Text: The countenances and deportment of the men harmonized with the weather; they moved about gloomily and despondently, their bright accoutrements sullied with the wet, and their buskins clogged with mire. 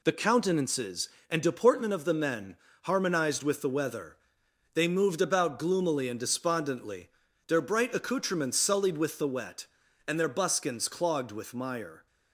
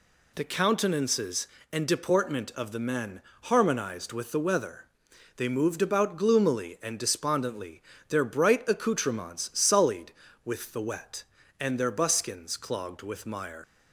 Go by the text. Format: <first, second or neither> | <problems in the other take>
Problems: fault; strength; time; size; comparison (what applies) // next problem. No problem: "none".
first | pauses between "men" and "harmonized"; slight; at 3.2 s; 0.22 s long; slight in the first // leaves "mire" unfinished; at 13.6 s; 105 ms